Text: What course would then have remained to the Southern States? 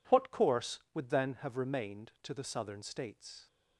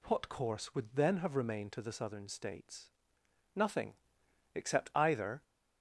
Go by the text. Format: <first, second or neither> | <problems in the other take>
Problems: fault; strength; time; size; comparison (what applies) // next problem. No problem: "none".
first | goes on to say "Nothing except either"; strong; from 3.5 s on; 1.8 s long